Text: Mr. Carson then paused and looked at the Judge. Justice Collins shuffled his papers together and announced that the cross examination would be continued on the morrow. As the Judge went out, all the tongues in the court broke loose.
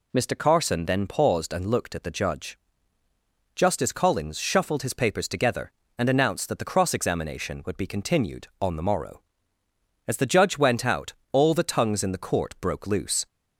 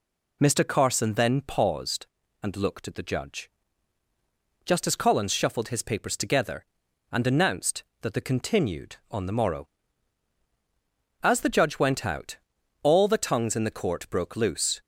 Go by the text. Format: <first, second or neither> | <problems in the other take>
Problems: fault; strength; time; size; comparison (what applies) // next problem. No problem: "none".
first | skips "cross examination would be"; at 8.2 s